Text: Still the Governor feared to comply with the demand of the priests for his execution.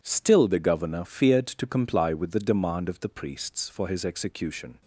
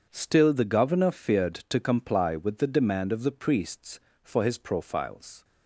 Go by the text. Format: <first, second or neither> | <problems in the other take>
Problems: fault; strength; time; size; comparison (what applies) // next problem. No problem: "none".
first | says "profiles" for "execution"; at 4.5 s